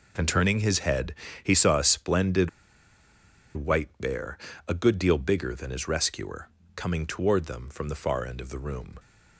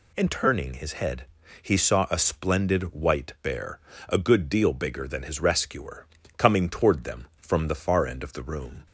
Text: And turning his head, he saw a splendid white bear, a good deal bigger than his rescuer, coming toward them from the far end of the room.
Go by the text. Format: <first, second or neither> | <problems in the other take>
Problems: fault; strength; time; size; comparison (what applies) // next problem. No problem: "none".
second | pauses between "splendid" and "white"; at 2.4 s; 1.0 s long